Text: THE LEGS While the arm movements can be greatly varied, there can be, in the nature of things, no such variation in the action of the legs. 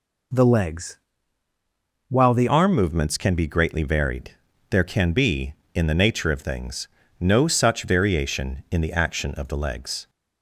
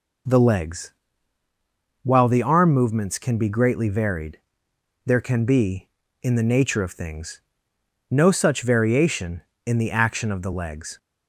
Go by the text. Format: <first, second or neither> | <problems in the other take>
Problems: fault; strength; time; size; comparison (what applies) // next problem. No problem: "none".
second | pauses between "LEGS" and "While"; at 0.9 s; 1.1 s long; also in the second // changes voice at "arm"; from 2.4 s on; 7.6 s long